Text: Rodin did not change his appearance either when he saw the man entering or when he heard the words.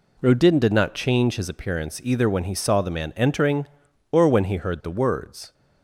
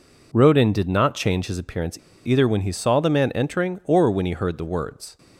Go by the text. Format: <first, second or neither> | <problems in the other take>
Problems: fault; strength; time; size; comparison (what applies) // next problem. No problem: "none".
first | pauses between "appearance" and "either"; slight; at 1.9 s; 0.27 s long